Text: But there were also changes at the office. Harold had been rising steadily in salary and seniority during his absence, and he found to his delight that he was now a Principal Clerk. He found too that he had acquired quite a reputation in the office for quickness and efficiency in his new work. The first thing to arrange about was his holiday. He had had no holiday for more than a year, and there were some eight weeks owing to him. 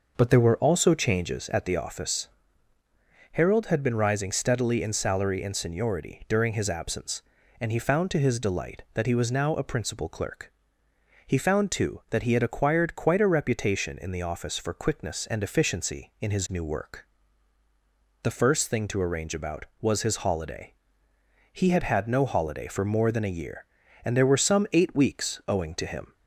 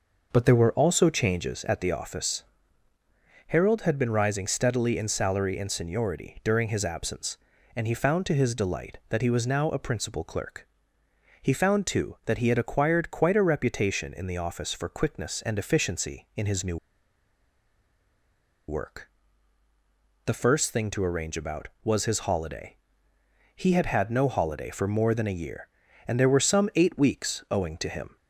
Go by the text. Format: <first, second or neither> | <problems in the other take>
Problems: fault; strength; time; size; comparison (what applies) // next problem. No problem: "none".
first | pauses between "new" and "work"; strong; at 16.7 s; 1.9 s long